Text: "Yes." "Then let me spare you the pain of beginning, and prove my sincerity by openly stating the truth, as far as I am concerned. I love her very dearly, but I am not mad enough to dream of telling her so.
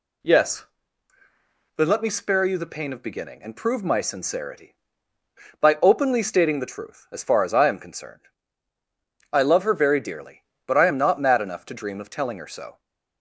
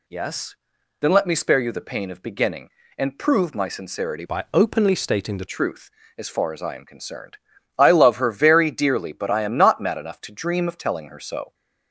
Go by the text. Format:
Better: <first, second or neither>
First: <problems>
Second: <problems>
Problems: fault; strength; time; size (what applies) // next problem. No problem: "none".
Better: first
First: none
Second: changes voice from "by" to "the"; from 4.2 to 5.4 s; 1.2 s long